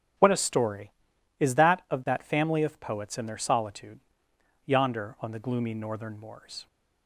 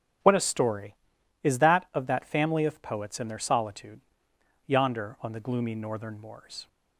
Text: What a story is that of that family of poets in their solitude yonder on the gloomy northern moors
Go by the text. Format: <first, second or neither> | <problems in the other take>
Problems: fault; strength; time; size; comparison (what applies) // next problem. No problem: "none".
neither | starts louder than the rest; strong; the same in both // pauses between "solitude" and "yonder"; noticeable; the same in both